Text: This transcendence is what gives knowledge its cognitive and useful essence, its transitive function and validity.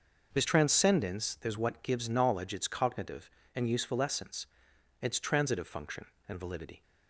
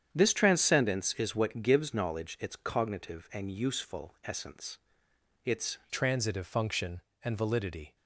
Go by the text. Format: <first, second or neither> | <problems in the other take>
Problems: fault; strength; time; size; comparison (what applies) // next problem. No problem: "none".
first | starts louder than the rest; strong; until 1.1 s; 8.5 dB // changes voice at "transitive"; from 5.8 s on; 2.1 s long